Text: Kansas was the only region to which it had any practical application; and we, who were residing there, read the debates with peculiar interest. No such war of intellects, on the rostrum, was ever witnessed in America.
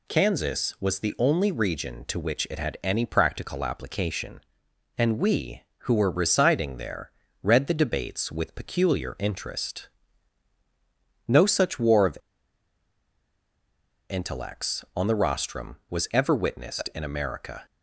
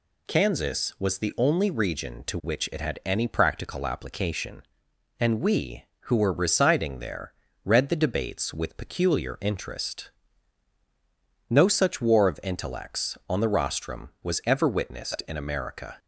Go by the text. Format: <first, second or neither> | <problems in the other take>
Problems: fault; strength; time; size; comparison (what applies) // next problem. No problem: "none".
second | pauses between "of" and "intellects"; strong; at 12.1 s; 1.9 s long